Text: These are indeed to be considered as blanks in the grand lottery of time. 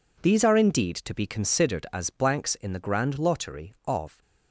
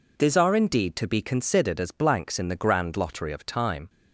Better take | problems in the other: second | stops before "time"; at 4.2 s

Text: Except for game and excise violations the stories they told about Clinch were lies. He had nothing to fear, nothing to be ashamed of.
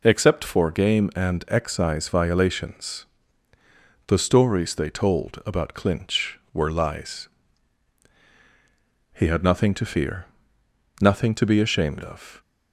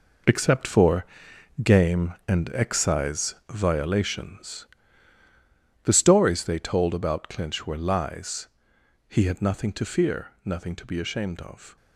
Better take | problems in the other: first | gets quieter; strong; throughout; 11 dB // pauses between "for" and "game"; noticeable; at 1.0 s; 0.58 s long // pauses between "excise" and "violations"; slight; at 3.3 s; 0.16 s long // pauses between "violations" and "the"; at 4.6 s; 1.1 s long; also in the first

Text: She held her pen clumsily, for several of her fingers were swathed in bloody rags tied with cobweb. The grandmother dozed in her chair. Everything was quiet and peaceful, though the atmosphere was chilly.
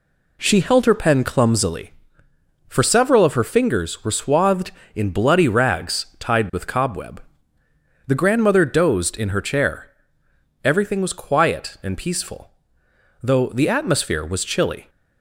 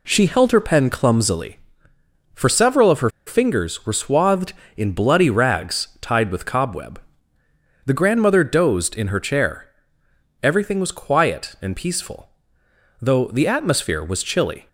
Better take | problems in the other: first | pauses between "her" and "fingers"; slight; at 3.1 s; 0.16 s long

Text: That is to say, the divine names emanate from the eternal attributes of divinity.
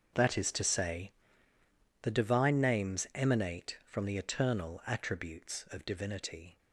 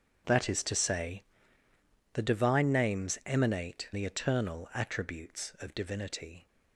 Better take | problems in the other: first | starts louder than the rest; strong; until 2.1 s; 7.5 dB; also in the first // skips "from"; at 3.9 s

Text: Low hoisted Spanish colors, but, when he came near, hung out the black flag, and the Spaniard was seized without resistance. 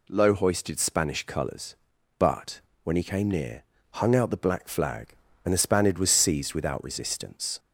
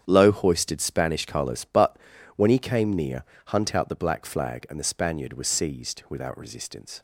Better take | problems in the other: first | starts louder than the rest; strong; until 1.0 s; 8.5 dB // says "hunt" for "hung"; at 3.4 s

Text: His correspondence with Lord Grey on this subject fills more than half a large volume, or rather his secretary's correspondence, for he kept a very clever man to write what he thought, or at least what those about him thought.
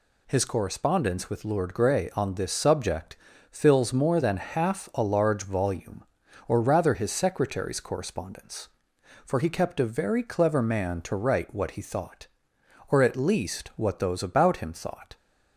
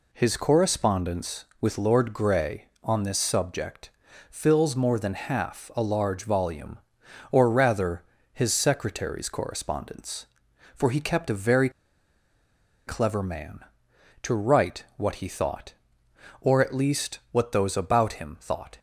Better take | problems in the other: first | pauses between "subject" and "fills"; at 3.8 s; 0.40 s long; slight in the first // pauses between "rather" and "his"; slight; at 8.0 s; 0.28 s long // pauses between "very" and "clever"; at 11.6 s; 1.1 s long

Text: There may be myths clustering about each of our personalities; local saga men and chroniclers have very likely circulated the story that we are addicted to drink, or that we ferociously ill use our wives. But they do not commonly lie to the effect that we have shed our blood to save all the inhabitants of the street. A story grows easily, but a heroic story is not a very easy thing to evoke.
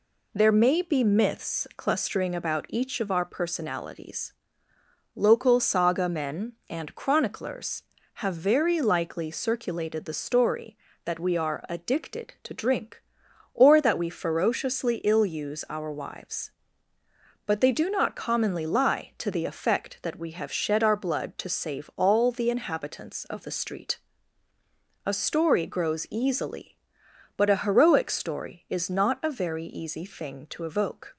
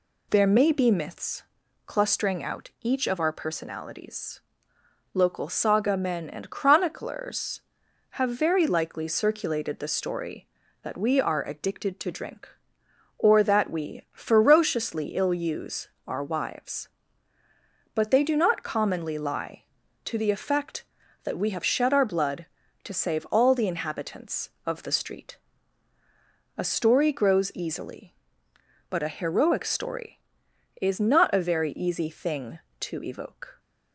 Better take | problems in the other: first | pauses between "myths" and "clustering"; at 1.4 s; 0.44 s long // says "out" for "about"; at 2.4 s // pauses between "use" and "our"; slight; at 15.8 s; 0.18 s long

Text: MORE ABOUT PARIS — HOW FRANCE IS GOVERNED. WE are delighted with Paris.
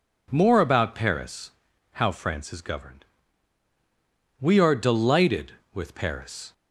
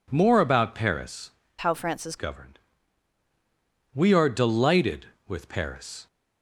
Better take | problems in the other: first | changes voice from "HOW" to "IS"; from 1.5 to 2.1 s; 0.6 s long

